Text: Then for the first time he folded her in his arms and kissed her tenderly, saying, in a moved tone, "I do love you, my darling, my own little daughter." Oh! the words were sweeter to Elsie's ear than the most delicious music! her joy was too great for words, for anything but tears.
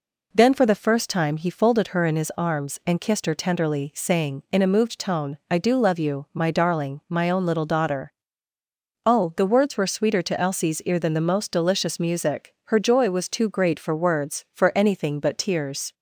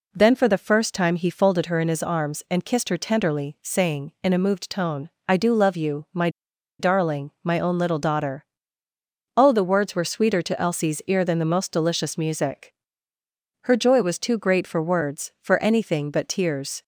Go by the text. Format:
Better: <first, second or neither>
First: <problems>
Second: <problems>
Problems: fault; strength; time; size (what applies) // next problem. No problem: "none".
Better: first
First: none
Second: pauses between "my" and "darling"; noticeable; at 6.2 s; 0.50 s long